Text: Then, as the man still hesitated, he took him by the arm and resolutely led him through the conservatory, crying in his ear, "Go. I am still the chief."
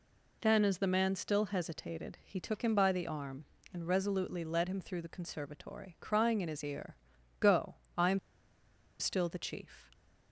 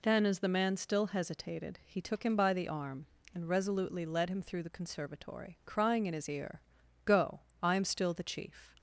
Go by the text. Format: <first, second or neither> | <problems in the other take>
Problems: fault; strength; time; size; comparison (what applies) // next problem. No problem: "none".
second | pauses between "am" and "still"; noticeable; at 8.1 s; 0.81 s long